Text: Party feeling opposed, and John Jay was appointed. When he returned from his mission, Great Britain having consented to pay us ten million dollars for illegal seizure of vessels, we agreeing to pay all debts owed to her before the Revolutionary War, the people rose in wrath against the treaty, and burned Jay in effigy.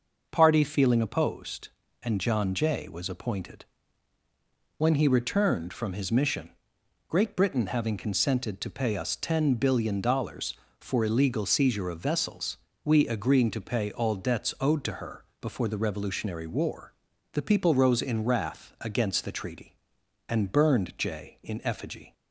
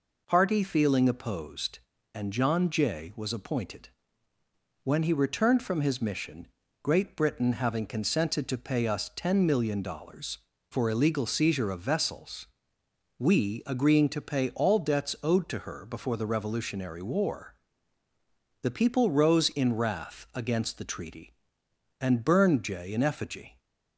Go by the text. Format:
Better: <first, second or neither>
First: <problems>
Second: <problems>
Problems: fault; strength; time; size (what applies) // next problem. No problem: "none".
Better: second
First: says "billion" for "million"; at 9.5 s // pauses between "her" and "before"; slight; at 15.2 s; 0.16 s long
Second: none